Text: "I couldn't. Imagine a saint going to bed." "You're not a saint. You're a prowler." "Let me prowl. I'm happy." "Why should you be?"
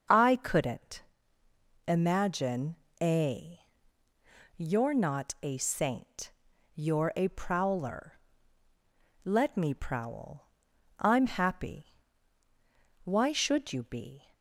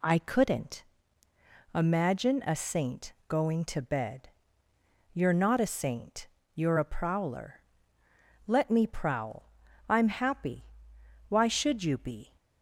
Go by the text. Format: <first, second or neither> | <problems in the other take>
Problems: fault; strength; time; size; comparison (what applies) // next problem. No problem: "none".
second | starts louder than the rest; noticeable; until 1.9 s; 6 dB // pauses between "Imagine" and "a"; slight; at 2.7 s; 0.22 s long // skips "saint going to bed"; at 4.0 s